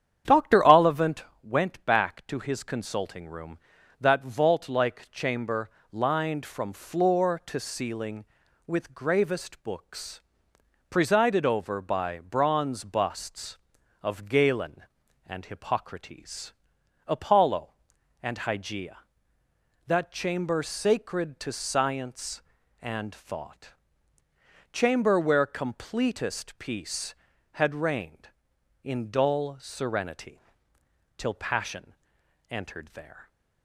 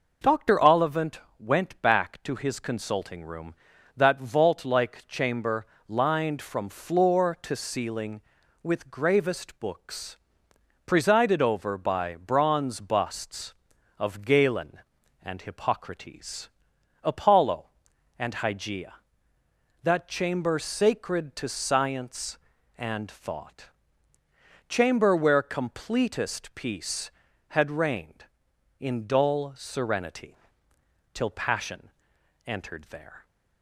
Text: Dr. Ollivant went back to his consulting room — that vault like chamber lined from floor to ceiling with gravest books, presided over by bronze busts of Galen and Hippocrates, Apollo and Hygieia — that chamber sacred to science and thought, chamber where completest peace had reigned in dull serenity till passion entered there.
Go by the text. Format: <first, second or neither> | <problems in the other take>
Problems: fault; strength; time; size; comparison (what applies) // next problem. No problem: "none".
second | starts louder than the rest; strong; until 1.5 s; 9 dB // pauses between "Ollivant" and "went"; slight; at 1.2 s; 0.22 s long; slight in the second // pauses between "chamber" and "lined"; slight; at 5.7 s; 0.22 s long; slight in the second // pauses between "serenity" and "till"; noticeable; at 30.3 s; 0.80 s long; noticeable in the second // pauses between "passion" and "entered"; noticeable; at 31.9 s; 0.56 s long; noticeable in the second